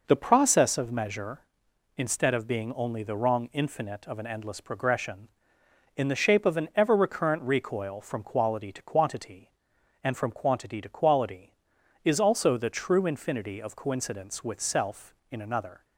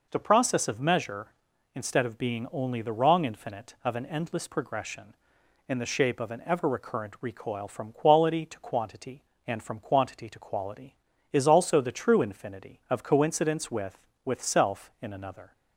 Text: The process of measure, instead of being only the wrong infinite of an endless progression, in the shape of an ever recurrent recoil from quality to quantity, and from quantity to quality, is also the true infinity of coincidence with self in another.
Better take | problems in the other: first | says "with" twice; at 14.2 s

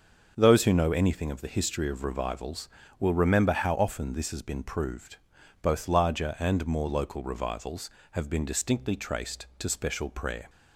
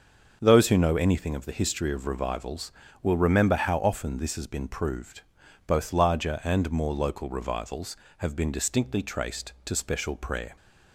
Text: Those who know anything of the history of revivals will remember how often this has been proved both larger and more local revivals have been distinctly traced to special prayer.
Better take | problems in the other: neither | starts louder than the rest; the same in both // pauses between "proved" and "both"; noticeable; the same in both

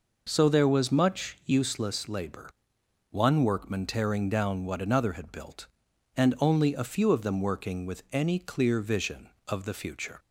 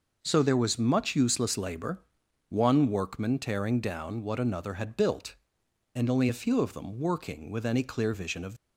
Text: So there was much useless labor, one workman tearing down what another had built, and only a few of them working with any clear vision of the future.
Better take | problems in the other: first | stops before "the future"; at 8.5 s

